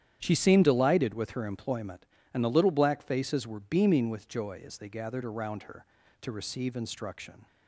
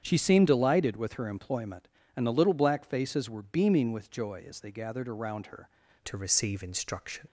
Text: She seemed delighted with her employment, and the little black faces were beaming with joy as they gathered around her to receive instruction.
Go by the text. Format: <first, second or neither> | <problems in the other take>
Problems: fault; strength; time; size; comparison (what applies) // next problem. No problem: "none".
first | starts louder than the rest; strong; until 1.0 s; 8.5 dB; strong in the first // changes voice at "to"; from 6.0 s on; 1.2 s long